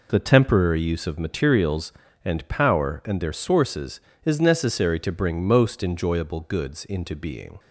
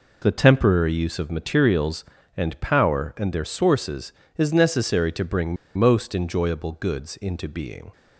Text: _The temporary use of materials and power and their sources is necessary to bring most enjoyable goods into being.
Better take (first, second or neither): first